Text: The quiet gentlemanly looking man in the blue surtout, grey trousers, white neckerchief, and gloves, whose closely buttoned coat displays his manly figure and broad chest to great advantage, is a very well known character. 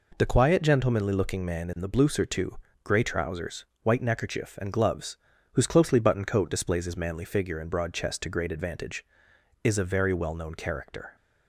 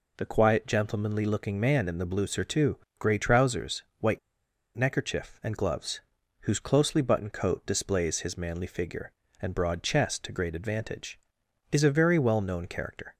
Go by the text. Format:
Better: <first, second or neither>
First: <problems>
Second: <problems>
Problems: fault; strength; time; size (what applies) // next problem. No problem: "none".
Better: first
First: none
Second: pauses between "white" and "neckerchief"; noticeable; at 4.1 s; 0.57 s long